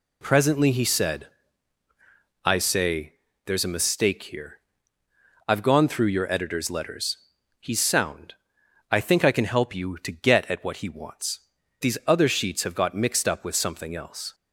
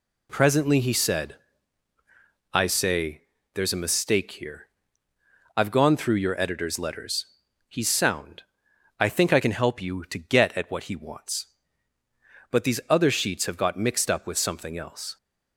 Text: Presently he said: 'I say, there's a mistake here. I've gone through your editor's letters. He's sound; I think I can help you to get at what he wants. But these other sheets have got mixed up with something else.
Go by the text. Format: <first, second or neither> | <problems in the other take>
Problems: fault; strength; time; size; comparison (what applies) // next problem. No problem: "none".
second | skips "But"; at 11.6 s